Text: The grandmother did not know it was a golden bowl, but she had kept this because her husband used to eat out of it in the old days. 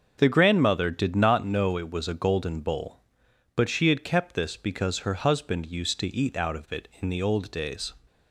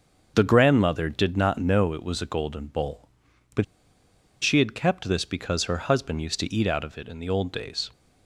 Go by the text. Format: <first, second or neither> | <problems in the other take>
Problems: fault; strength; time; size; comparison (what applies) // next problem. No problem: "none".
first | starts louder than the rest; until 1.3 s; 6.5 dB; also in the first // pauses between "but" and "she"; noticeable; at 3.6 s; 0.79 s long